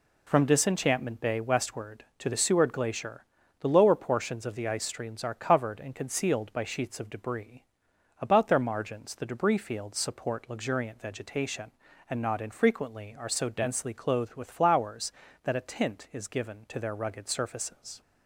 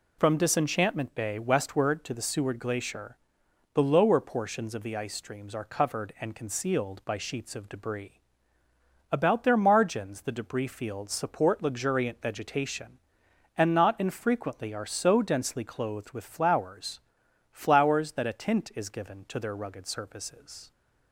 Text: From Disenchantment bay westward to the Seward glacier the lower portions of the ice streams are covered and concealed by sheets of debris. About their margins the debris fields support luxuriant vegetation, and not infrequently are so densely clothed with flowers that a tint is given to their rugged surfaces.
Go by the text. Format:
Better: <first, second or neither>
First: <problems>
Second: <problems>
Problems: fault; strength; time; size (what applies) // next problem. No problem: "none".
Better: first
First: pauses between "glacier" and "the"; slight; at 3.2 s; 0.36 s long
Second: pauses between "glacier" and "the"; noticeable; at 3.1 s; 0.56 s long // says "flowers" twice; at 17.4 s